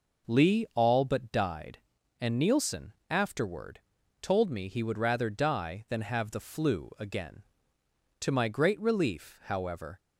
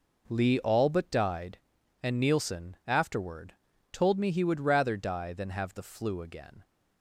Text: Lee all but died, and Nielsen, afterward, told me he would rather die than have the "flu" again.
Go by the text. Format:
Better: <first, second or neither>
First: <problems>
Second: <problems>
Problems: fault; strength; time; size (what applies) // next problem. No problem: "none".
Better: second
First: goes on to say "To my great relief however"; strong; from 8.2 s on; 1.7 s long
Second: none